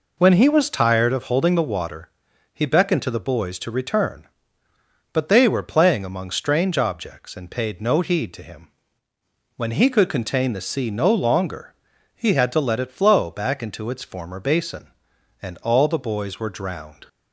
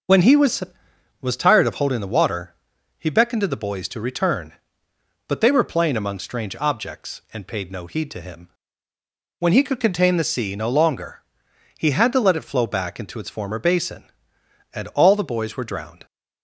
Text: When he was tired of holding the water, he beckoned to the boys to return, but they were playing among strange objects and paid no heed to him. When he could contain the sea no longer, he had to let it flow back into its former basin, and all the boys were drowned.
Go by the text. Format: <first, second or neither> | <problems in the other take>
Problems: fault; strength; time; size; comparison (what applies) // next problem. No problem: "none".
first | says "was" twice; at 1.2 s